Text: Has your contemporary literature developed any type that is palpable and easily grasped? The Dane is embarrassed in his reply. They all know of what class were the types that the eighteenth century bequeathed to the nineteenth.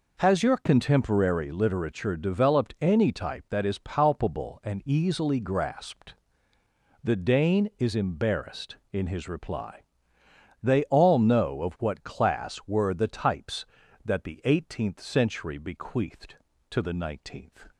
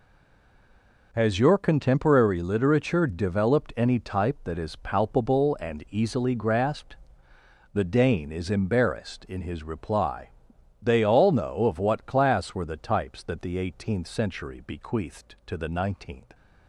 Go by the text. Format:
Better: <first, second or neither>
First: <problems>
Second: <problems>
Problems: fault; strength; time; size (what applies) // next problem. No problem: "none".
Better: first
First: none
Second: stays silent before the first word; until 1.1 s; 1.1 s long